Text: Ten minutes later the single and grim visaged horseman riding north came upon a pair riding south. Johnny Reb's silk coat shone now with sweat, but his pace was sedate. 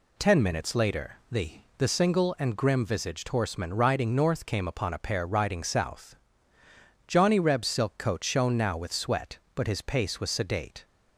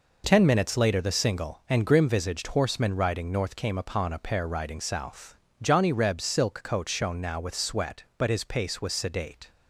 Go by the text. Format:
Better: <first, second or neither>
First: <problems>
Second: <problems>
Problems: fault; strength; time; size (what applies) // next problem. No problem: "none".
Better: second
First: says "the" twice; at 1.7 s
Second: none